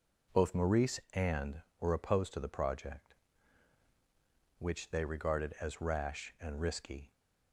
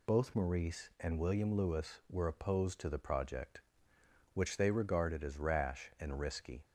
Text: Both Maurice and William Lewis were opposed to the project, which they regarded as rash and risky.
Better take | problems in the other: second | skips "William Lewis"; at 1.7 s

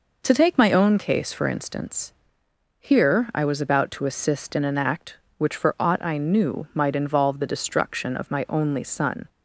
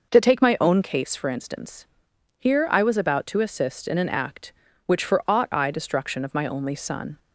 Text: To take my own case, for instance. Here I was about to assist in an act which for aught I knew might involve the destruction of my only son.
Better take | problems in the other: first | skips "knew might involve the"; at 5.7 s

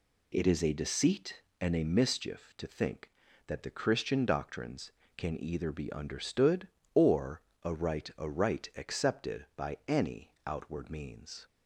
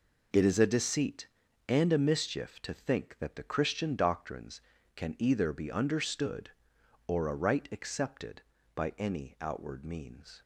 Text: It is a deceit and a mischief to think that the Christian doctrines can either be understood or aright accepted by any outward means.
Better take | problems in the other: second | pauses between "or" and "aright"; slight; at 7.4 s; 0.22 s long // says "aright" twice; at 8.1 s // pauses between "any" and "outward"; slight; at 10.3 s; 0.16 s long

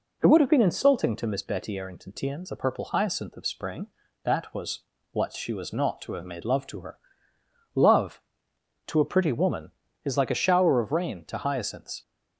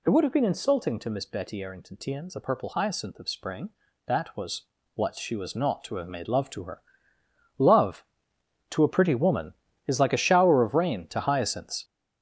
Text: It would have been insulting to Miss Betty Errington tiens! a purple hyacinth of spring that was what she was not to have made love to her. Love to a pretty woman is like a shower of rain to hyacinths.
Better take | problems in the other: first | gets louder; strong; throughout; 8 dB // pauses between "was" and "what"; slight; at 4.6 s; 0.32 s long; slight in the first

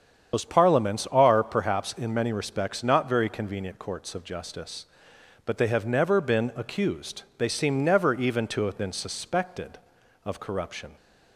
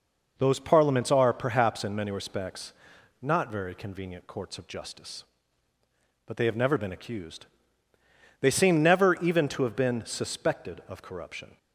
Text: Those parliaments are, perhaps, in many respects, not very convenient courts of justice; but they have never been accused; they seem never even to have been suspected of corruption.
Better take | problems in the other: second | loses the start of "Those"; at 0.3 s; 60 ms // starts louder than the rest; strong; until 1.4 s; 8 dB

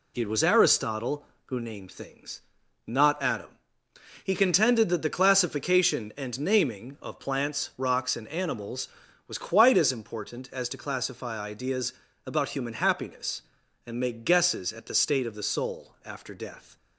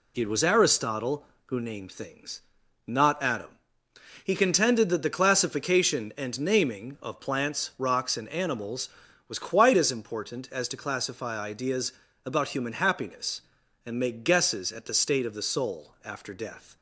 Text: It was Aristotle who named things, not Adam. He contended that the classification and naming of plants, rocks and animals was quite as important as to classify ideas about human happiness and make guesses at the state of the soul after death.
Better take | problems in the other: neither | pauses between "ideas" and "about"; slight; the same in both

